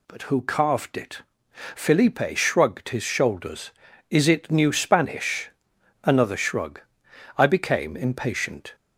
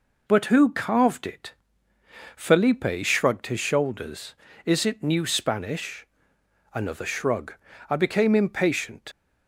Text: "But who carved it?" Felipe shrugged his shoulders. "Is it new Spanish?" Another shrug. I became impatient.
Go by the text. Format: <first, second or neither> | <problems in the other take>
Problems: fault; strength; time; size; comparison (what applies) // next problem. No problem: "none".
first | leaves "impatient" unfinished; at 9.1 s; 50 ms